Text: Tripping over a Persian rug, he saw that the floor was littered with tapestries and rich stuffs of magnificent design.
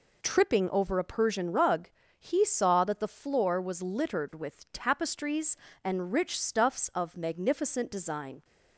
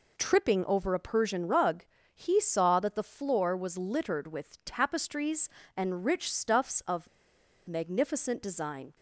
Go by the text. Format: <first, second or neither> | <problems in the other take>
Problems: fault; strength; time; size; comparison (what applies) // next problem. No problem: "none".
first | pauses between "of" and "magnificent"; noticeable; at 7.0 s; 0.61 s long